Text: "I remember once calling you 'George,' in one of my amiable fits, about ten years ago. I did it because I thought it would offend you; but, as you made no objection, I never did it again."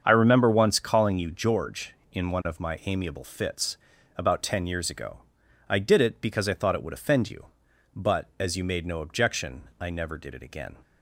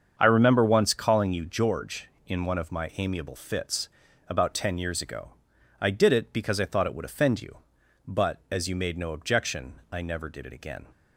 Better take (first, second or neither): neither